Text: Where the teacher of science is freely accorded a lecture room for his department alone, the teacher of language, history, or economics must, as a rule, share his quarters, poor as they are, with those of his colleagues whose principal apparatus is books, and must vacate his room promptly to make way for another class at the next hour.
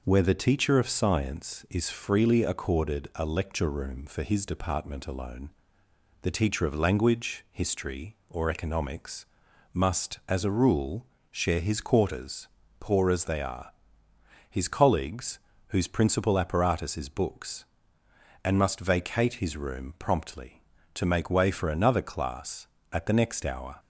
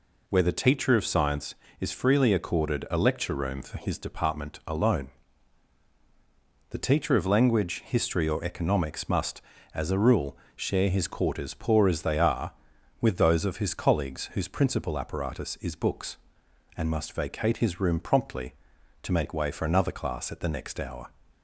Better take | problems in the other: second | pauses between "economics" and "must"; noticeable; at 9.2 s; 0.48 s long // skips "with those of"; at 14.1 s // pauses between "colleagues" and "whose"; slight; at 15.3 s; 0.30 s long

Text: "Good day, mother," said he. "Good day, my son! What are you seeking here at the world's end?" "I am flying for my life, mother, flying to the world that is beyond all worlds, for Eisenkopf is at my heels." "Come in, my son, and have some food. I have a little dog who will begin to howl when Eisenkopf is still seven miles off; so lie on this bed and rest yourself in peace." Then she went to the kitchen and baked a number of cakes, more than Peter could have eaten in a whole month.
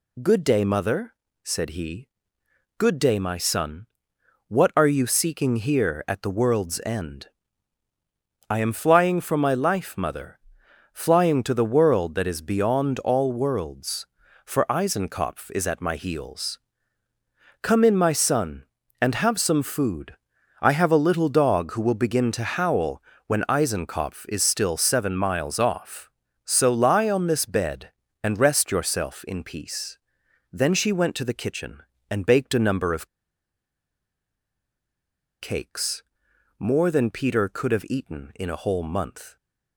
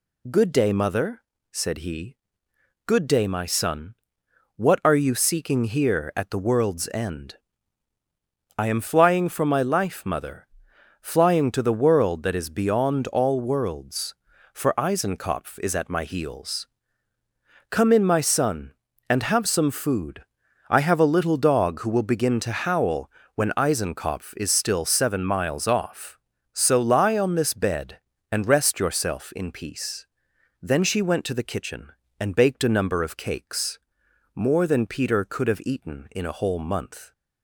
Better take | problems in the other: second | pauses between "howl" and "when"; slight; at 23.0 s; 0.26 s long; slight in the second // pauses between "of" and "cakes"; strong; at 33.0 s; 2.3 s long

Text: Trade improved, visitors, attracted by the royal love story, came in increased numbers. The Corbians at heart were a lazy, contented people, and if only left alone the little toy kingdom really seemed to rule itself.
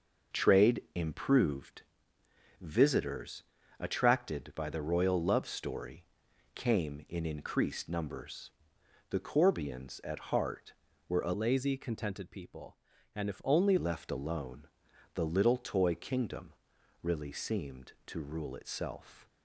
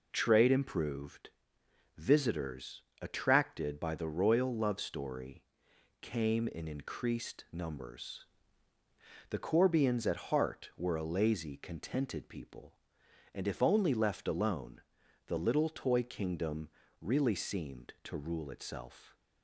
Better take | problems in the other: second | changes voice from "lazy" to "only"; from 11.3 to 13.7 s; 2.4 s long // pauses between "alone" and "the"; noticeable; at 14.6 s; 0.50 s long; noticeable in the second // pauses between "kingdom" and "really"; noticeable; at 16.5 s; 0.50 s long; slight in the second

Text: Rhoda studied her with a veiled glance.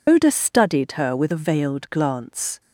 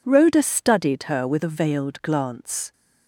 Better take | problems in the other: second | loses the start of "Rhoda"; at 0.0 s; 135 ms

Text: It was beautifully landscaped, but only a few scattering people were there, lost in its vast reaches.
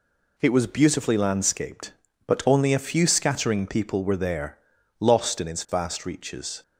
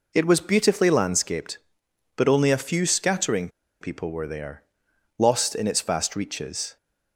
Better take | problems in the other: first | pauses between "scattering" and "people"; slight; at 3.4 s; 0.32 s long

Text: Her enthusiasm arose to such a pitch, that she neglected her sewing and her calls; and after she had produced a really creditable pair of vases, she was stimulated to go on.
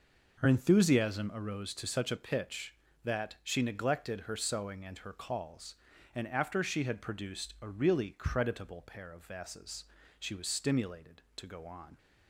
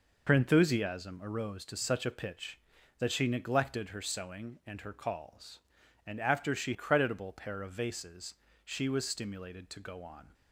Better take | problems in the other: first | skips "had produced a really"; at 6.7 s

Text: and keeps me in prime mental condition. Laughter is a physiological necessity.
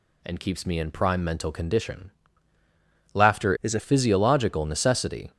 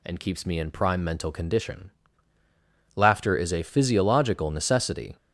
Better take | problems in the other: second | changes voice from "is" to "a"; from 3.6 to 3.7 s; 0.1 s long

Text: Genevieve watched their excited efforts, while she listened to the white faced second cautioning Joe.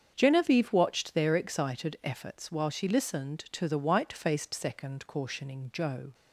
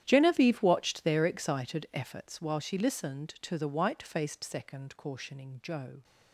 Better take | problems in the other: first | gets quieter; strong; throughout; 18.5 dB // starts louder than the rest; strong; until 1.0 s; 11 dB; strong in the first

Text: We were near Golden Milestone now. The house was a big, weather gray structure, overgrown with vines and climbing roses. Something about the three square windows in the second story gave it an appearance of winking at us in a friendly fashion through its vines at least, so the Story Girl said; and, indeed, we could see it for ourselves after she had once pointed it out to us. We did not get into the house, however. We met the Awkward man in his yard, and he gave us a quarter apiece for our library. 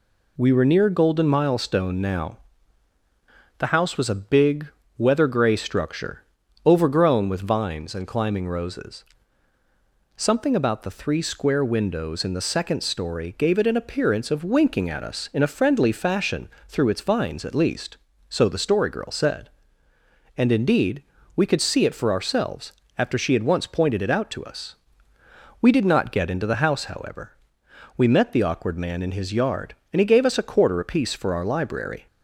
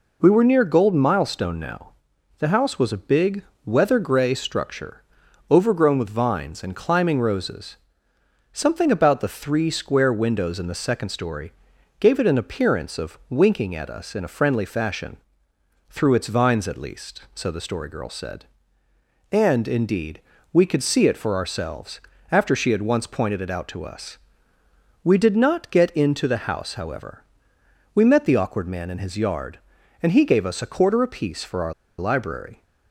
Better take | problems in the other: first | pauses between "story" and "gave"; noticeable; at 11.5 s; 0.46 s long // pauses between "fashion" and "through"; noticeable; at 15.1 s; 0.72 s long; slight in the first // pauses between "ourselves" and "after"; slight; at 21.9 s; 0.32 s long; slight in the first // pauses between "our" and "library"; slight; at 31.7 s; 0.25 s long

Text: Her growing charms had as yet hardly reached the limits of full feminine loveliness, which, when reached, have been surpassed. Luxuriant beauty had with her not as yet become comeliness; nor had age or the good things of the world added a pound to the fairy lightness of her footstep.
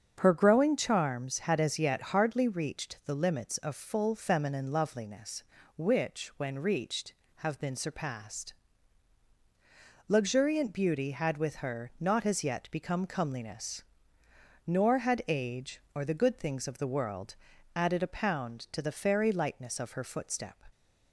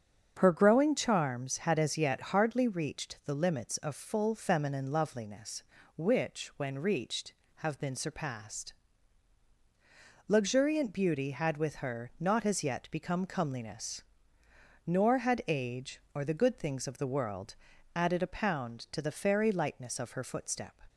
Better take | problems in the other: neither | starts louder than the rest; strong; the same in both // pauses between "world" and "added"; the same in both

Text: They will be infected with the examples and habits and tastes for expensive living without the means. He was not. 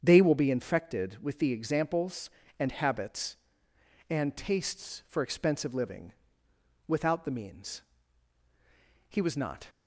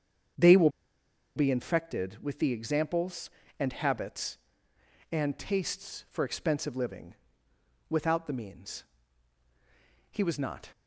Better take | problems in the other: first | starts louder than the rest; strong; until 2.0 s; 7.5 dB; strong in the first // pauses between "will" and "be"; noticeable; at 0.6 s; 0.66 s long // pauses between "living" and "without"; noticeable; at 7.1 s; 0.74 s long; noticeable in the first

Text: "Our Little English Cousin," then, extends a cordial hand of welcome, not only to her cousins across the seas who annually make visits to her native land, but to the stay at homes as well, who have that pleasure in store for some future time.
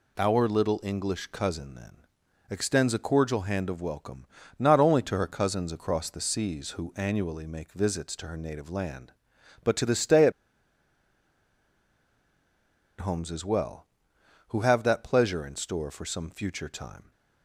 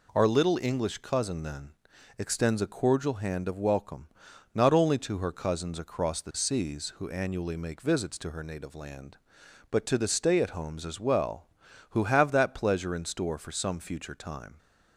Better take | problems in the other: second | pauses between "at" and "homes"; strong; at 10.3 s; 2.6 s long

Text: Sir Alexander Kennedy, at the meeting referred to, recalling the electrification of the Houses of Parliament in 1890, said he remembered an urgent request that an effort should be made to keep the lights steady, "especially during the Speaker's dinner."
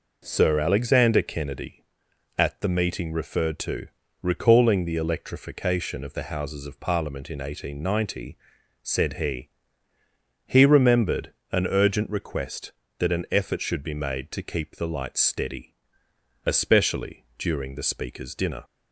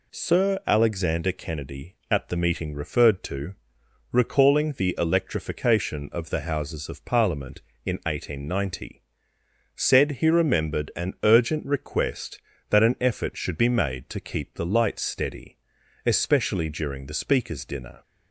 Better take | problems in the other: second | says "he" twice; at 10.4 s // pauses between "remembered" and "an"; slight; at 11.3 s; 0.18 s long

